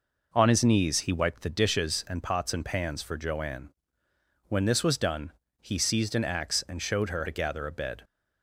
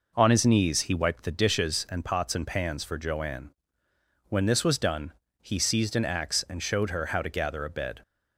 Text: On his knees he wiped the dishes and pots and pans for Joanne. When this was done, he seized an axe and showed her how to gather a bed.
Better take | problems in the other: second | skips "how"; at 7.2 s

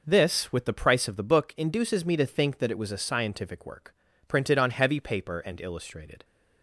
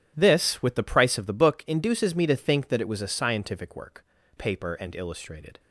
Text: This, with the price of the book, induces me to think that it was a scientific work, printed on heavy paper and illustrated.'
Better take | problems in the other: first | starts louder than the rest; strong; until 1.1 s; 10.5 dB // skips "printed on heavy"; at 4.2 s

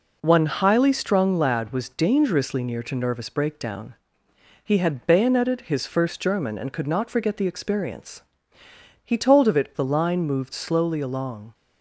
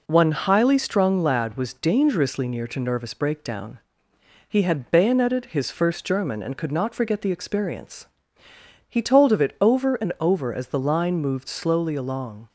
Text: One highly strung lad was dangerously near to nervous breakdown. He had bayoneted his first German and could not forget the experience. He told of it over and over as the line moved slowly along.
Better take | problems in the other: second | skips "over and over as"; at 9.7 s

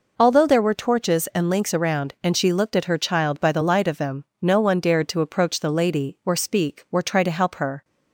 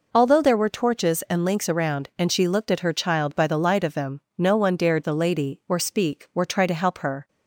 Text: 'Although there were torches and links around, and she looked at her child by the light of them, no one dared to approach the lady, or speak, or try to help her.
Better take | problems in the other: first | skips "to approach"; at 5.0 s

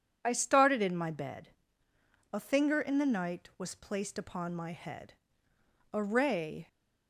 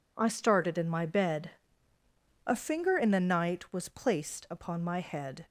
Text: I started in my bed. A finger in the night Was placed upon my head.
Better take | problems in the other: second | goes on to say "A ray"; noticeable; from 5.9 s on; 0.74 s long

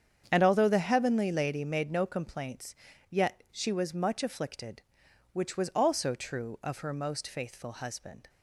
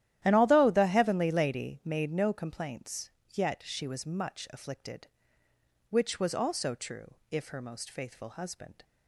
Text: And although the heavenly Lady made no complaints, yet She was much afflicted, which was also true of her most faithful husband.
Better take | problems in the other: first | starts louder than the rest; strong; until 1.2 s; 12.5 dB; strong in the first // says "if" for "of"; at 7.2 s

